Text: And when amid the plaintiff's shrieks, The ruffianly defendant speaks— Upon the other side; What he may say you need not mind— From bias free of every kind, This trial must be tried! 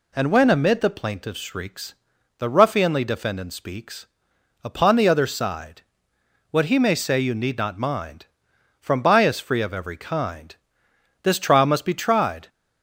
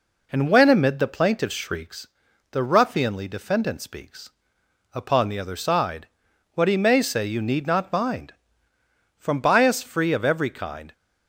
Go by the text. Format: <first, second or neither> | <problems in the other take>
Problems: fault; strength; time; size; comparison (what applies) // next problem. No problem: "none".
first | stops before "This trial must be tried"; at 10.9 s